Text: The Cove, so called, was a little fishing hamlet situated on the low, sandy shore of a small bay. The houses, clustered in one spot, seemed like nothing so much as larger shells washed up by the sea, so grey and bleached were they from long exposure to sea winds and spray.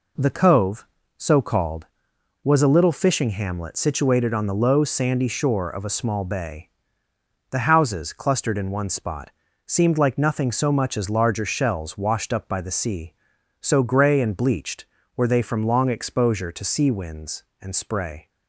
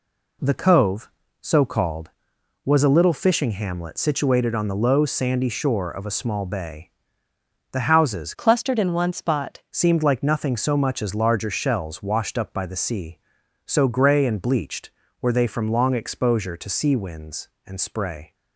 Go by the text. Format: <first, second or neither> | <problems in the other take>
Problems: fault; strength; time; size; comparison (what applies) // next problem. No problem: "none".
first | changes voice from "clustered" to "spot"; from 8.3 to 9.6 s; 1.3 s long